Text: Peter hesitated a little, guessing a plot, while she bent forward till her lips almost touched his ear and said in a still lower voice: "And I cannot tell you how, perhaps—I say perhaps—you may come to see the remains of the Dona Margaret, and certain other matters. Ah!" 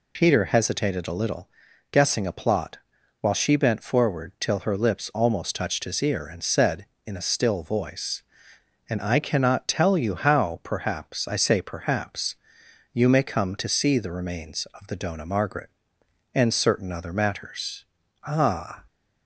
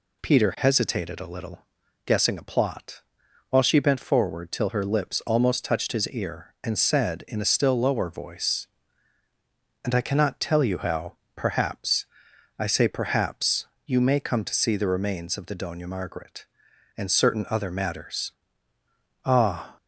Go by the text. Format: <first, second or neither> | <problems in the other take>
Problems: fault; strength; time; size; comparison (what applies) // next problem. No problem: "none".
second | skips "lower"; at 7.6 s